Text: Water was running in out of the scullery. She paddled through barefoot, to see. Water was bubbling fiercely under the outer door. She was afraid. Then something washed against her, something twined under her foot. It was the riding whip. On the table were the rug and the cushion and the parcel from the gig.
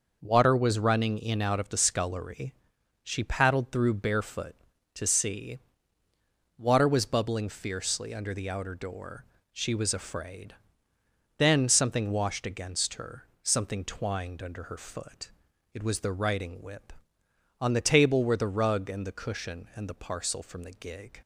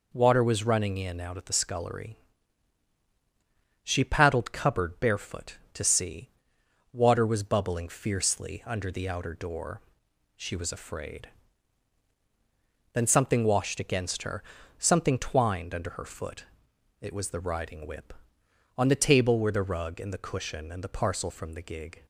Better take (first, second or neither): first